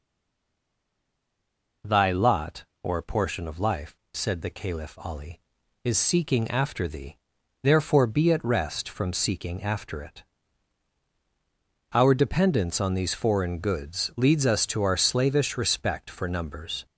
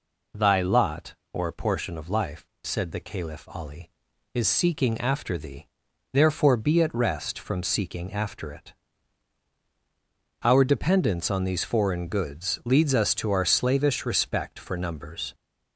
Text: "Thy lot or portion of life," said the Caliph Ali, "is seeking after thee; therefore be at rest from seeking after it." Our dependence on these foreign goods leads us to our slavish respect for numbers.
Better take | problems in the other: second | stays silent before the first word; noticeable; until 1.8 s; 1.8 s long

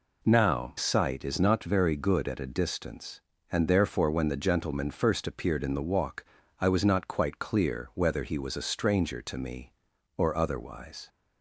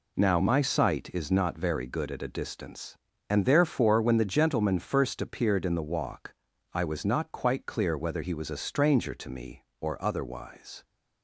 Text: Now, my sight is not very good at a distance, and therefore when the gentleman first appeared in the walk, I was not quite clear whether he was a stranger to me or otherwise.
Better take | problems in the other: second | skips "my"; at 0.7 s

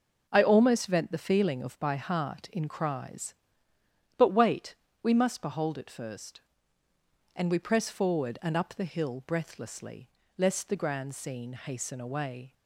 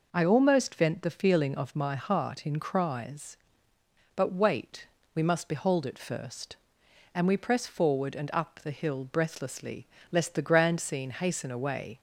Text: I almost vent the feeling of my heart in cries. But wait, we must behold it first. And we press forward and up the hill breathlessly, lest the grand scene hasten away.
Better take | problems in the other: second | says "by" for "my"; at 1.7 s

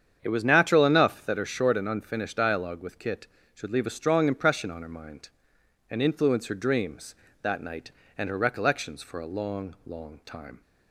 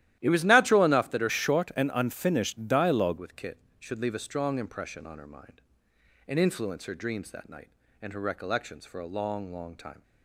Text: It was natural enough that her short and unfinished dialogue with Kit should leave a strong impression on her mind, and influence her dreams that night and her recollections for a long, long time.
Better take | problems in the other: first | starts louder than the rest; strong; until 1.2 s; 13 dB; strong in the first // changes voice from "short" to "dialogue"; from 1.2 to 3.1 s; 1.9 s long

